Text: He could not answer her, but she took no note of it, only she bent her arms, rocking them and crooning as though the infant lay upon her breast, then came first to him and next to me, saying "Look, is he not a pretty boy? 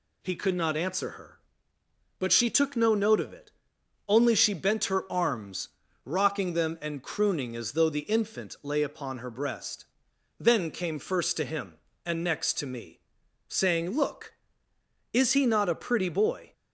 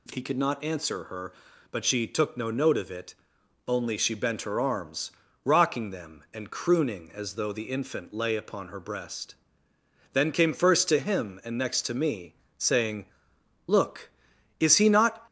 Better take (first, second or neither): first